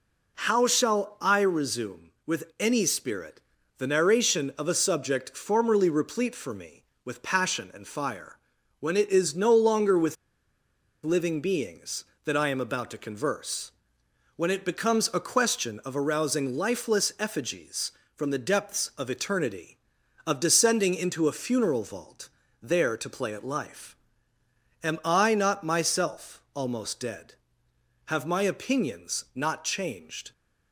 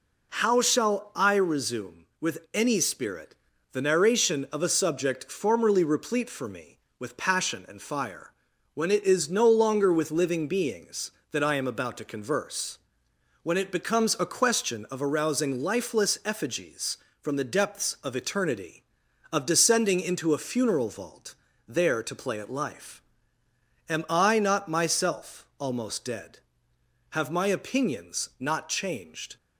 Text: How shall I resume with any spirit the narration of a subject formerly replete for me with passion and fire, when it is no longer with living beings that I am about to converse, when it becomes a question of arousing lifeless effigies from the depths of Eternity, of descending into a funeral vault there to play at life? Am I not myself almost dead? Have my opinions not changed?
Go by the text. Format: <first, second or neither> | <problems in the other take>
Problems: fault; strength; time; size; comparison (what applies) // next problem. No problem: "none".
second | pauses between "spirit" and "the"; at 3.3 s; 0.38 s long; also in the second // pauses between "with" and "living"; noticeable; at 10.1 s; 0.88 s long // pauses between "vault" and "there"; slight; at 22.2 s; 0.34 s long; slight in the second